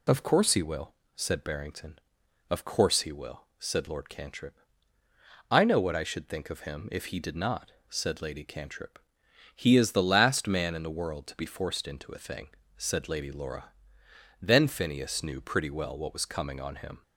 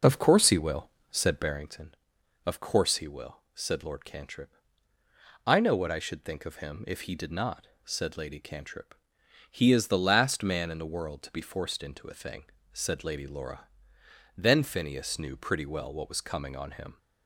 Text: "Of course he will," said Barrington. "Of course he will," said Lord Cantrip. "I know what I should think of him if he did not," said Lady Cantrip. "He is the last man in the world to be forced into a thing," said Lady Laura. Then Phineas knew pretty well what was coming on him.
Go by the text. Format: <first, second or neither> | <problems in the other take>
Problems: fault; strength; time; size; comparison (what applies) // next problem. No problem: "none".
first | starts louder than the rest; noticeable; until 1.6 s; 5 dB